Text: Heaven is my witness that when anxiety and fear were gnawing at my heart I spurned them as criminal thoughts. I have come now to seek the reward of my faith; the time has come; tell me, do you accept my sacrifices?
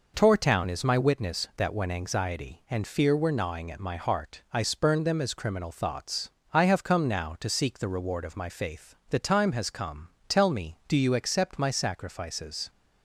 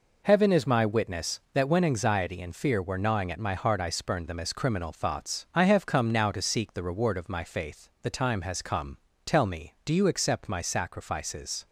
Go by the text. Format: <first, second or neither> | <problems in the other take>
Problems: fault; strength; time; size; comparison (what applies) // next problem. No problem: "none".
second | says "Tortown" for "Heaven"; at 0.1 s